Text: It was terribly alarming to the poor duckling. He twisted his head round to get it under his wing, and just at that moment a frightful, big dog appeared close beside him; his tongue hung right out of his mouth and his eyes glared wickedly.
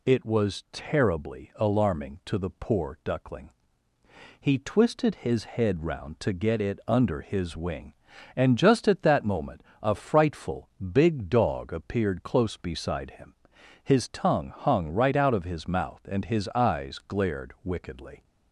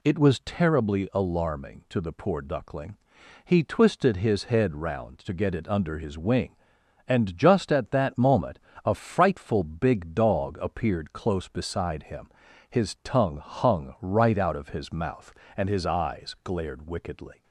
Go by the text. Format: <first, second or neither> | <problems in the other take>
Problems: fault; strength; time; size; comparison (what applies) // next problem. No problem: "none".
neither | pauses between "moment" and "a"; slight; the same in both